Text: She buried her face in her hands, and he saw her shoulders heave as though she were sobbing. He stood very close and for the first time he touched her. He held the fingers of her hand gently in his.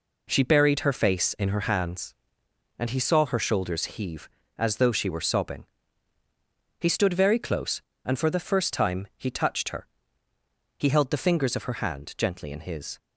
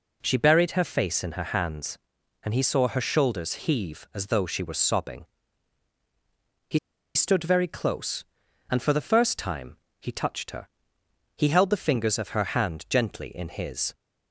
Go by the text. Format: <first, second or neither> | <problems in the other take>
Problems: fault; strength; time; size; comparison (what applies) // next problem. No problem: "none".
first | pauses between "He" and "stood"; at 6.7 s; 0.36 s long // pauses between "time" and "he"; slight; at 9.7 s; 0.20 s long